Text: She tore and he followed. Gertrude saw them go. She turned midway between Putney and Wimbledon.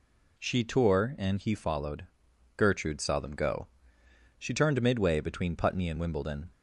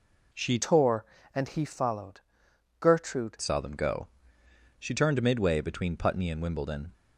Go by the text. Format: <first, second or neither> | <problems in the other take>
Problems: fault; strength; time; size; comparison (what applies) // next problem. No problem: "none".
first | changes voice from "tore" to "Gertrude"; from 0.5 to 3.3 s; 2.8 s long